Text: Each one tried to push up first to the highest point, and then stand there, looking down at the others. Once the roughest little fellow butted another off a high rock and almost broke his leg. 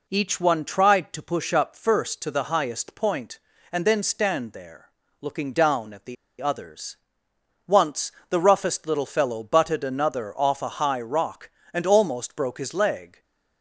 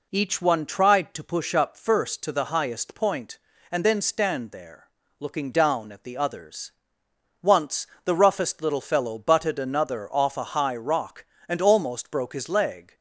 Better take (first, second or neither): second